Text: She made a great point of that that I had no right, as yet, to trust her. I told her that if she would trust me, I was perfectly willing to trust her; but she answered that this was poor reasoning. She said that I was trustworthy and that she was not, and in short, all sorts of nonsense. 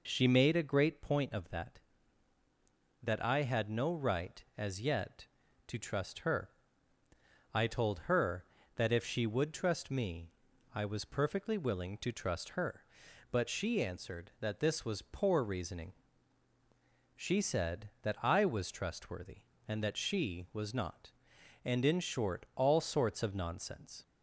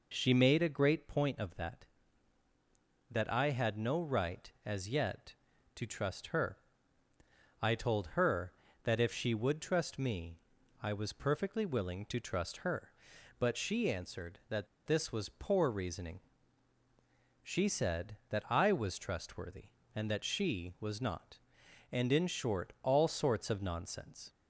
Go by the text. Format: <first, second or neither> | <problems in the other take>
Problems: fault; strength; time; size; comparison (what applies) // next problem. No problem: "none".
first | pauses between "that" and "this"; slight; at 14.6 s; 0.19 s long